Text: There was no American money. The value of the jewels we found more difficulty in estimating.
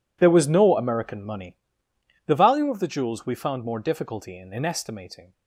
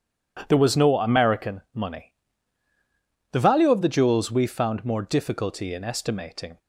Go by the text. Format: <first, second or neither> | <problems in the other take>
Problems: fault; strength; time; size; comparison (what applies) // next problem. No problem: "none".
second | says "in" twice; at 4.5 s